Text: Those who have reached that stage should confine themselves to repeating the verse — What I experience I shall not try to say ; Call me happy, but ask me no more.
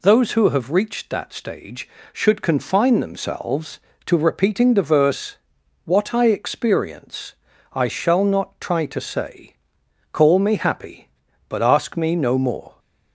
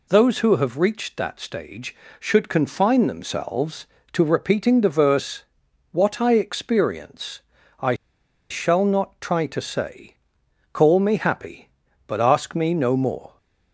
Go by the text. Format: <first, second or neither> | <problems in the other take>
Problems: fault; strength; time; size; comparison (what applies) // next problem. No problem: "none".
first | pauses between "experience" and "I"; at 7.3 s; 0.40 s long; also in the first // pauses between "I" and "shall"; noticeable; at 7.9 s; 0.55 s long